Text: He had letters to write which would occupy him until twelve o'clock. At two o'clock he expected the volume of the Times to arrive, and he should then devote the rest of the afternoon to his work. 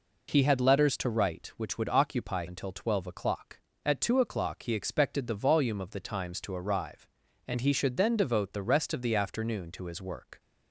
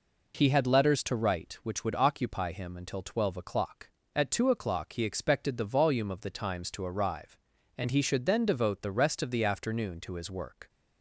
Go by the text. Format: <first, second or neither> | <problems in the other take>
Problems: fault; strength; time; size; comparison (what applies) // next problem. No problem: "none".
second | skips "him"; at 2.4 s